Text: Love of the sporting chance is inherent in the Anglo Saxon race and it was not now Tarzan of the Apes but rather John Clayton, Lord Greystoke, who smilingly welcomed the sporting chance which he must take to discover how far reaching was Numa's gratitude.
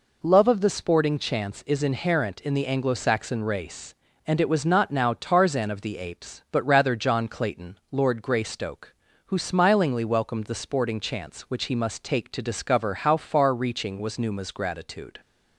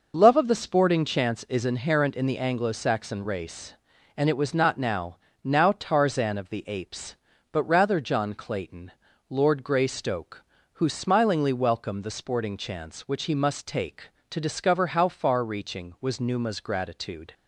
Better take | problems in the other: first | says "now" twice; at 5.4 s

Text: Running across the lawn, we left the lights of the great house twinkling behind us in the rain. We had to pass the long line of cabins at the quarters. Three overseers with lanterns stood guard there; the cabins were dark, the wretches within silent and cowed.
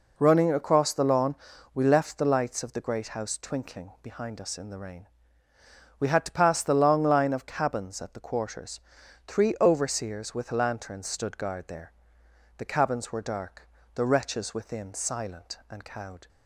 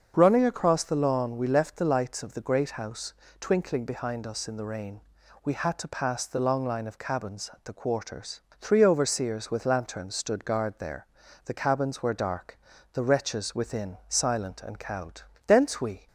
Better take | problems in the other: first | starts louder than the rest; until 1.1 s; 6.5 dB // pauses between "house" and "twinkling"; slight; at 3.1 s; 0.28 s long // goes on to say "Thence we"; from 15.4 s on; 0.60 s long

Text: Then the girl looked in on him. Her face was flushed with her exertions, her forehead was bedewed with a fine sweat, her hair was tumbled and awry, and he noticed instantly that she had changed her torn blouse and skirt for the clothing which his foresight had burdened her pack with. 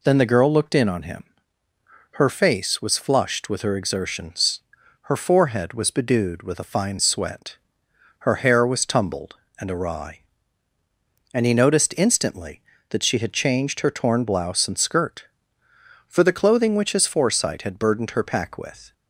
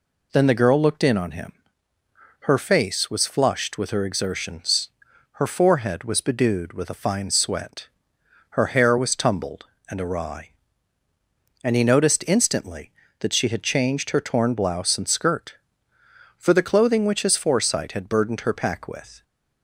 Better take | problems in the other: neither | none

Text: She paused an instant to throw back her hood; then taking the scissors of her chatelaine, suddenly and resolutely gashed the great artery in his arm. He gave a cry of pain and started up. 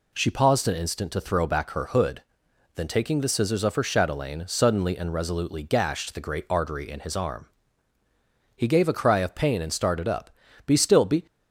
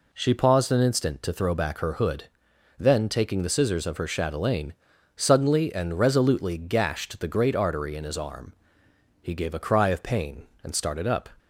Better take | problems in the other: second | goes on to say "Be still be"; from 10.6 s on; 0.58 s long

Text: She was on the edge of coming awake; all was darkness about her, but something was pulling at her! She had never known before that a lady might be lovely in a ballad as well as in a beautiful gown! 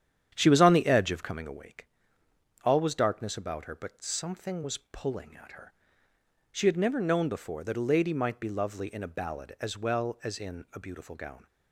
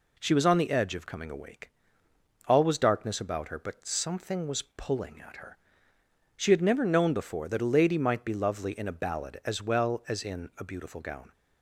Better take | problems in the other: second | starts louder than the rest; strong; until 1.6 s; 9.5 dB

